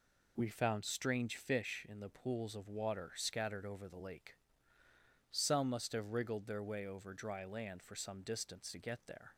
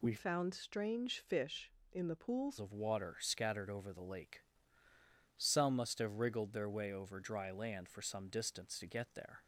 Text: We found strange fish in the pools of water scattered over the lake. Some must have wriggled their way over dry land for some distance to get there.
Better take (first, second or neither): first